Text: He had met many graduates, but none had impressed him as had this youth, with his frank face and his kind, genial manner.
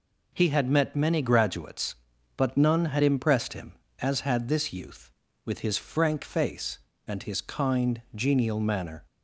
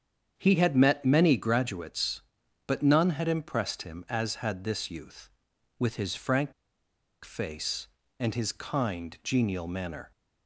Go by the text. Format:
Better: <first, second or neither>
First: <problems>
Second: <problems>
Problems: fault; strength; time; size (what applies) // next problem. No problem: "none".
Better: first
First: none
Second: starts louder than the rest; strong; until 1.3 s; 8 dB // pauses between "frank" and "face"; noticeable; at 6.5 s; 0.72 s long